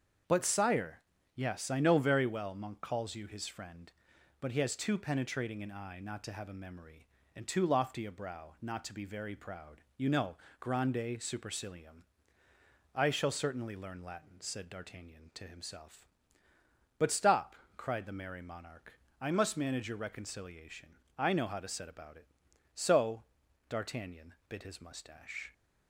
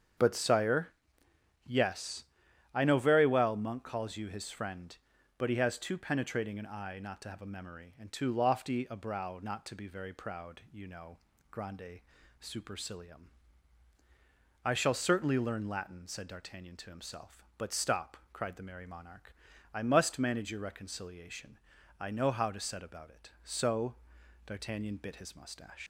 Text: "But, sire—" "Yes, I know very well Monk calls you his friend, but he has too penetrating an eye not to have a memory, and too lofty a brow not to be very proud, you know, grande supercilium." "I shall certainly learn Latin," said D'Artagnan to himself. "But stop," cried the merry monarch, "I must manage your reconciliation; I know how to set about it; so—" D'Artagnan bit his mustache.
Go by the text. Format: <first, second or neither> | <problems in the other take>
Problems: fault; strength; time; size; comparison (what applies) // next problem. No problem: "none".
first | starts louder than the rest; strong; until 1.9 s; 7.5 dB; also in the first // pauses between "grande" and "supercilium"; at 12.0 s; 0.40 s long // leaves "mustache" unfinished; at 25.8 s; 100 ms